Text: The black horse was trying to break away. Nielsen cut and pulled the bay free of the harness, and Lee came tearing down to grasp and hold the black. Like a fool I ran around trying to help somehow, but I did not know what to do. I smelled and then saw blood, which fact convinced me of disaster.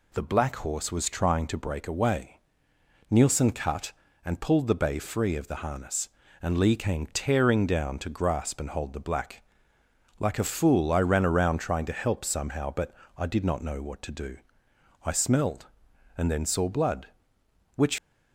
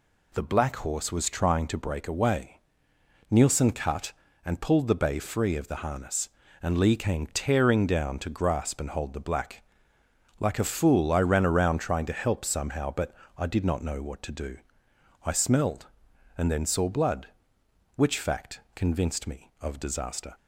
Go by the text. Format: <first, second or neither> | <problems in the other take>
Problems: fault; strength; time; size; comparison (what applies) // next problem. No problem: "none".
second | pauses between "but" and "I"; slight; at 12.9 s; 0.24 s long; slight in the second // stops before "fact convinced me of disaster"; at 17.9 s